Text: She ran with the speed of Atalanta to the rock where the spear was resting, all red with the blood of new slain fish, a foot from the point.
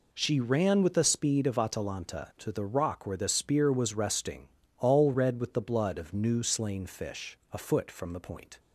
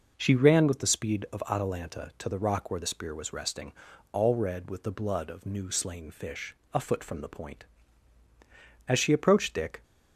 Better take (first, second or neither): first